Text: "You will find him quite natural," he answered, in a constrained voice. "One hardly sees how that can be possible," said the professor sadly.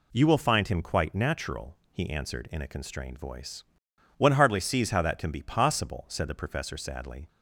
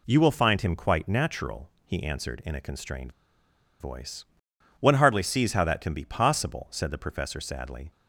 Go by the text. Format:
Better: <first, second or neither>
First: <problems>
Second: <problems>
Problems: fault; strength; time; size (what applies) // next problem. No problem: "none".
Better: first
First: none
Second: pauses between "constrained" and "voice"; noticeable; at 3.1 s; 0.69 s long